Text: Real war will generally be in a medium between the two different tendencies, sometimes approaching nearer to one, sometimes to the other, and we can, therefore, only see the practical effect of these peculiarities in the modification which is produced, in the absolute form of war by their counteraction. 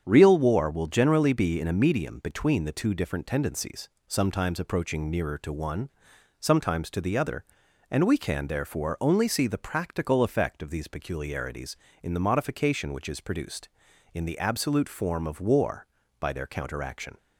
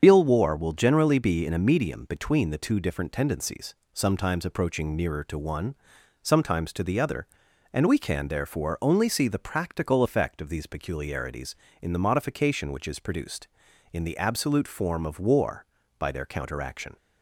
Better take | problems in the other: first | loses the start of "Real"; at 0.0 s; 115 ms // starts louder than the rest; strong; until 1.0 s; 7.5 dB; strong in the first

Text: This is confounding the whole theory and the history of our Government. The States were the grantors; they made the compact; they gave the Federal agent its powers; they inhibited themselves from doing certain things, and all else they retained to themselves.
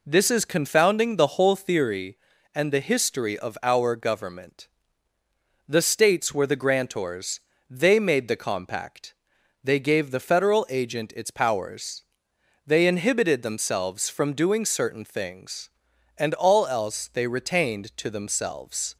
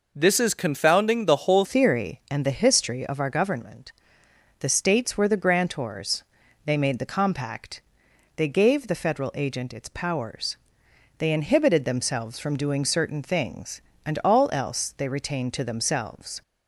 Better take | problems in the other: first | changes voice at "theory"; from 1.6 s on; 14.8 s long

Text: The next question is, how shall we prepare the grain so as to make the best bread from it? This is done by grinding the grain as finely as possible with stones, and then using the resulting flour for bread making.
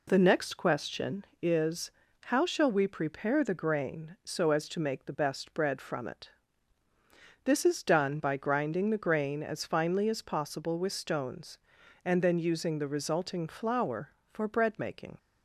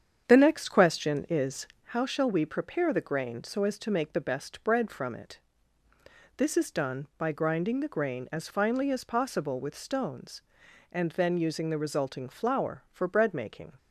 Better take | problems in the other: first | starts louder than the rest; strong; until 1.9 s; 8 dB

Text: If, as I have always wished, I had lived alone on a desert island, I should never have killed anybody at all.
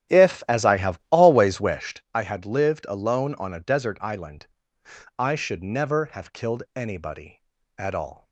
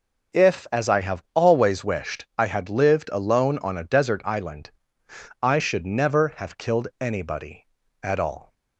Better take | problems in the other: second | starts louder than the rest; strong; until 1.9 s; 12 dB

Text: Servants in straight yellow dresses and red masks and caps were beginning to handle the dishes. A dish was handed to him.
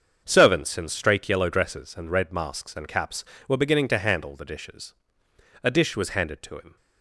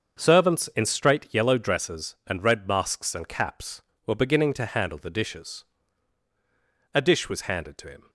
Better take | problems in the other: neither | starts louder than the rest; the same in both

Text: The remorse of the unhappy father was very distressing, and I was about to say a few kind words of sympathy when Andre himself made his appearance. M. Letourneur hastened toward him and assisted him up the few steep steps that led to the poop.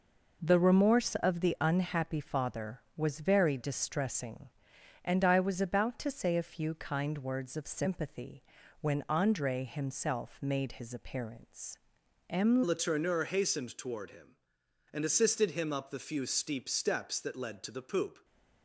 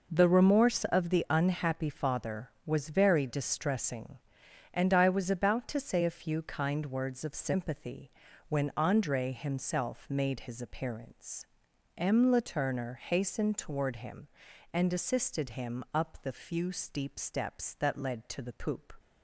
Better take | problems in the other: second | pauses between "sympathy" and "when"; at 8.4 s; 0.38 s long; also in the second // changes voice at "Letourneur"; from 12.6 s on; 5.6 s long

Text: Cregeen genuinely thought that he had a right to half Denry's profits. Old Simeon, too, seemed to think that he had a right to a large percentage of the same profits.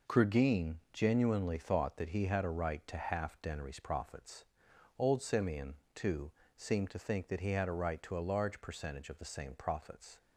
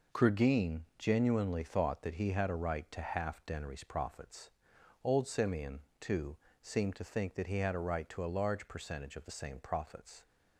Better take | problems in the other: neither | pauses between "Cregeen" and "genuinely"; slight; the same in both

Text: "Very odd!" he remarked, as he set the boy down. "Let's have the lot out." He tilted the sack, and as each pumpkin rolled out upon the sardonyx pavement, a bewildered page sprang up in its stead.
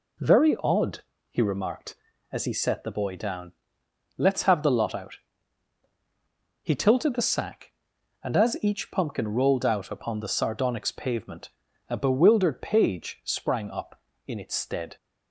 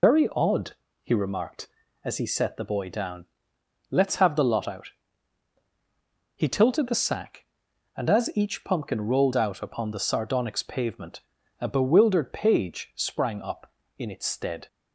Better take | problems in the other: first | loses the start of "Very"; at 0.0 s; 110 ms

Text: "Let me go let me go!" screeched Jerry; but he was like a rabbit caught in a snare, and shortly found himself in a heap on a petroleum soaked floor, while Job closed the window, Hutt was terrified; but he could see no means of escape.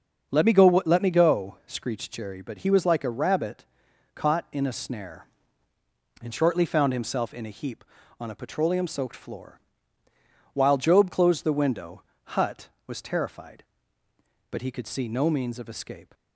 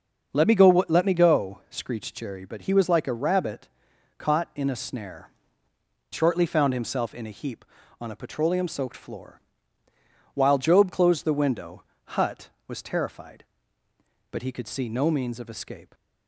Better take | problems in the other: first | starts louder than the rest; until 1.3 s; 6.5 dB; also in the first // pauses between "rabbit" and "caught"; noticeable; at 3.6 s; 0.50 s long; noticeable in the first // skips "and"; at 5.7 s

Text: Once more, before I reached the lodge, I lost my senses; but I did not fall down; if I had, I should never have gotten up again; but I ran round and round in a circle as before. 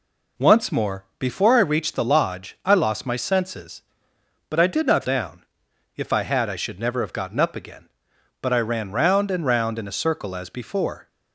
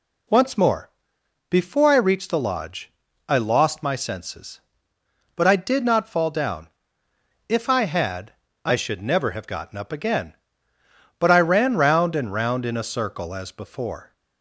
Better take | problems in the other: second | skips "fall"; at 5.0 s

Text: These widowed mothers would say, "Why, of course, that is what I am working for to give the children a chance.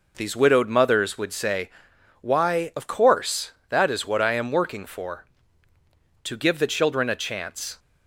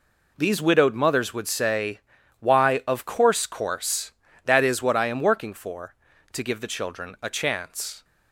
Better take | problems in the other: first | says "course" twice; at 3.4 s

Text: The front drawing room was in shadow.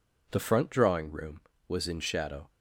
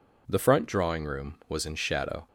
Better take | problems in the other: neither | none

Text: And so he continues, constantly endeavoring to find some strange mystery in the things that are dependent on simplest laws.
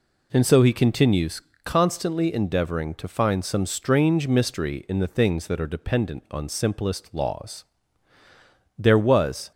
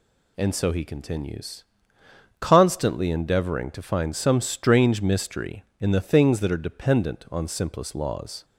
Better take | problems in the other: second | goes on to say "There was"; noticeable; from 8.7 s on; 0.74 s long

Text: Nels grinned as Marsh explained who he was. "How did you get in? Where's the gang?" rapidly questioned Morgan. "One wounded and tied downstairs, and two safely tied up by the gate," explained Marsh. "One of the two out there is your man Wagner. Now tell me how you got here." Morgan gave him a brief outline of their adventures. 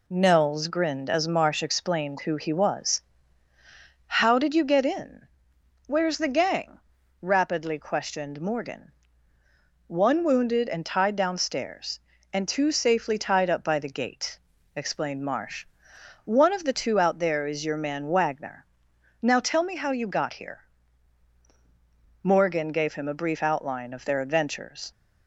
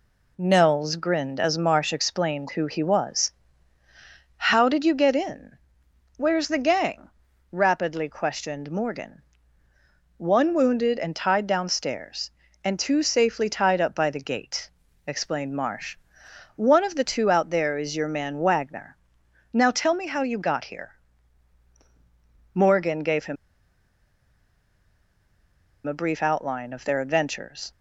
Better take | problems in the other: first | pauses between "him" and "a"; strong; at 23.3 s; 2.5 s long

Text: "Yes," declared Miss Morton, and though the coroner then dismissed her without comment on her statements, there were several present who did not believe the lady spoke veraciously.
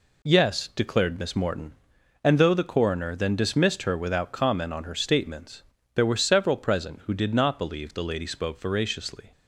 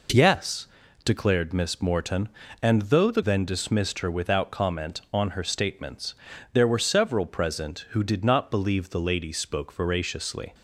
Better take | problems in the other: first | skips "coroner"; at 3.2 s

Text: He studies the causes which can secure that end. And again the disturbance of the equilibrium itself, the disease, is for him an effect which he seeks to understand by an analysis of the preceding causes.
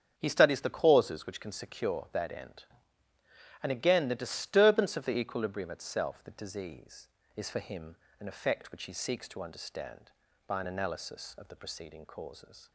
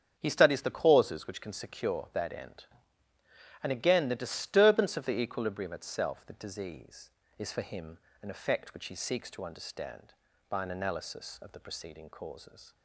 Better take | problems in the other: neither | starts louder than the rest; strong; the same in both // pauses between "him" and "an"; slight; the same in both

